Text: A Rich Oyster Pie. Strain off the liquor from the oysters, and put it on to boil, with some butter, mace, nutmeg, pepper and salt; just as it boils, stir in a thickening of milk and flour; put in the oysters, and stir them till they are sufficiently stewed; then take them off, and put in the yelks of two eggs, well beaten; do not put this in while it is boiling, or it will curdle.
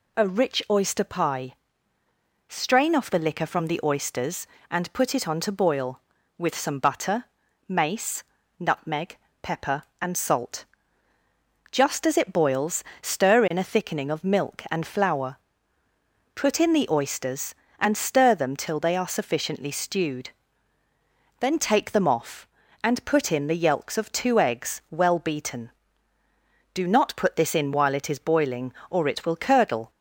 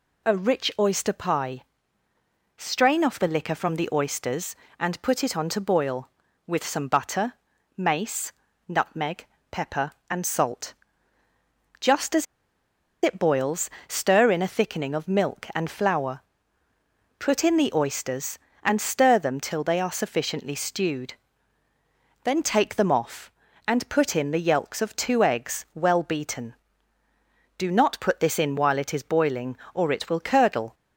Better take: first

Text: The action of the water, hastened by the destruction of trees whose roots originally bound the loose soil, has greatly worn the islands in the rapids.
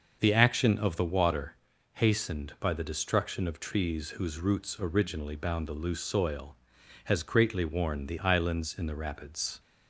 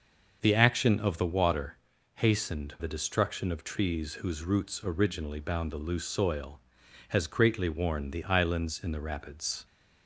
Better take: first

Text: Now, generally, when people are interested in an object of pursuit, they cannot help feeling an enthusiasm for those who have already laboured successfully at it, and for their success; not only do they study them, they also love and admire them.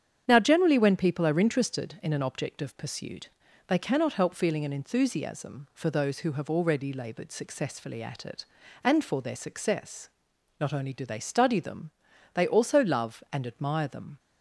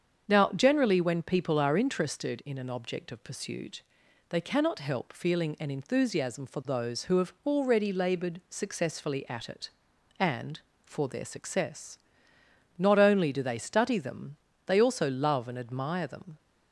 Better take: neither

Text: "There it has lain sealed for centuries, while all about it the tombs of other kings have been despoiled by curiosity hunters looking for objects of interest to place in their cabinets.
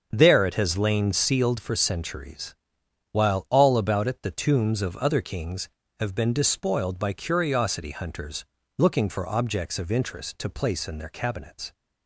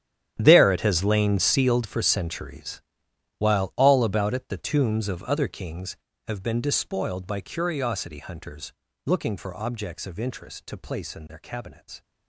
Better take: first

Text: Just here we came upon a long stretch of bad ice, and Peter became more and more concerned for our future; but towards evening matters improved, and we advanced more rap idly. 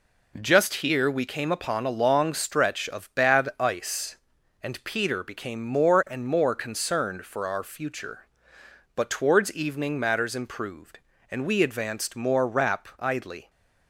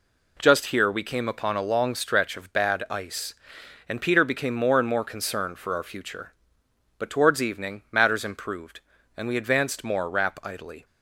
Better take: neither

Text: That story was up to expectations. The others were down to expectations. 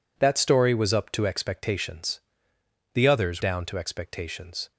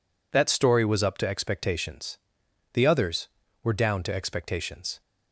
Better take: second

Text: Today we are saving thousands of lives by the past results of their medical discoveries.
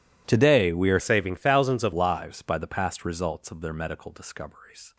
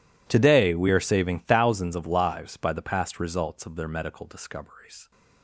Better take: second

